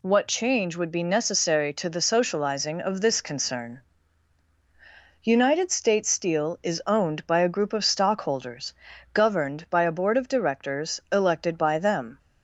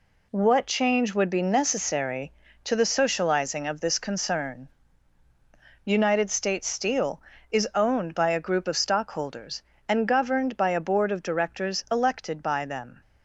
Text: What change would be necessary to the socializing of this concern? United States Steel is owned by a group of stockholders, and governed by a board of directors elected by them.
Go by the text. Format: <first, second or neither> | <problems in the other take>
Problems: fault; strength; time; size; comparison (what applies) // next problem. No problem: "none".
second | skips "and"; at 8.9 s